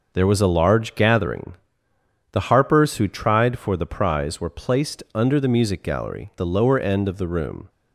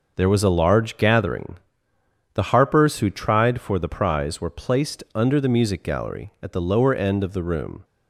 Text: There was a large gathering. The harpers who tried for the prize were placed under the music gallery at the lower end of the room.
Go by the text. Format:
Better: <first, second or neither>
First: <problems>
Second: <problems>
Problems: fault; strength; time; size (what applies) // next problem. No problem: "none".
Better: second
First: skips "at"; at 6.3 s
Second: none